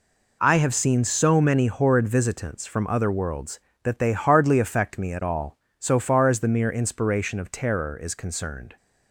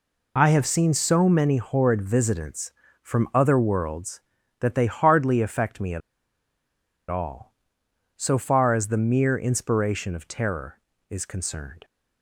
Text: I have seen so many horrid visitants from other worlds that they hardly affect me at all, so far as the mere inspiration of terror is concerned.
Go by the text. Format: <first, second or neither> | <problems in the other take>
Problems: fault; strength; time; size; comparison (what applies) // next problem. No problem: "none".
first | pauses between "at" and "all"; at 6.0 s; 1.1 s long